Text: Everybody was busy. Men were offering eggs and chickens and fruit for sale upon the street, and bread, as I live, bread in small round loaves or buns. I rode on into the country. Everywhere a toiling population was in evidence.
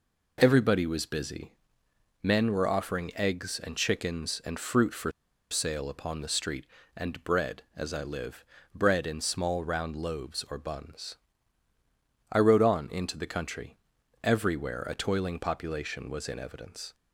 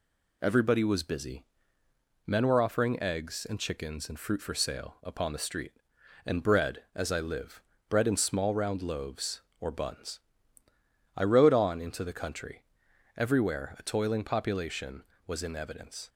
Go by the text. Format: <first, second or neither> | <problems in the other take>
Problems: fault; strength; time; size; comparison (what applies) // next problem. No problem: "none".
second | pauses between "for" and "sale"; at 5.1 s; 0.39 s long